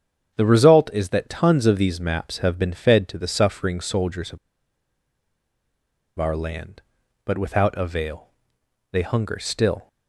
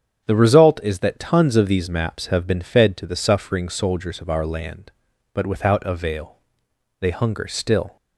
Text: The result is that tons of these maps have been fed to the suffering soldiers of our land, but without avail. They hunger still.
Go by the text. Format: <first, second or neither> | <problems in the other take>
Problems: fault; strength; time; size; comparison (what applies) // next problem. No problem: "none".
second | starts louder than the rest; strong; until 1.4 s; 8.5 dB; strong in the second // pauses between "of" and "our"; strong; at 4.3 s; 1.8 s long